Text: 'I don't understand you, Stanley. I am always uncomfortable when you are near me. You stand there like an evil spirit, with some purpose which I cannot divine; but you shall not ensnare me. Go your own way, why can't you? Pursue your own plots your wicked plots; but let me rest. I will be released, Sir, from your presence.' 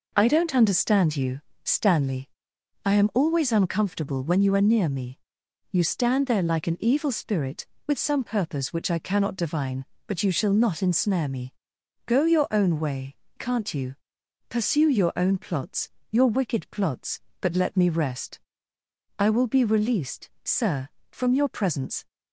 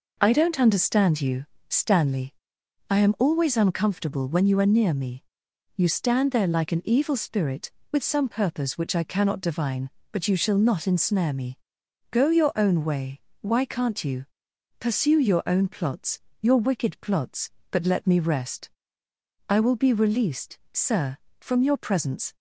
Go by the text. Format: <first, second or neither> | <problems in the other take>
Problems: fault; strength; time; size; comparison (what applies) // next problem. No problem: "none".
second | skips "why"; at 13.2 s // pauses between "plots" and "your"; slight; at 15.8 s; 0.20 s long; slight in the second